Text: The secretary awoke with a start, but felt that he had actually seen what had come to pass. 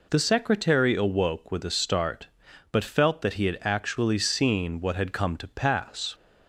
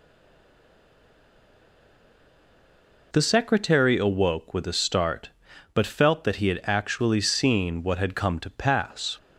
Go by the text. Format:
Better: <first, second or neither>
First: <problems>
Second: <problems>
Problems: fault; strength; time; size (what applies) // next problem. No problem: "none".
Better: first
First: none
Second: stays silent before the first word; strong; until 3.1 s; 3.1 s long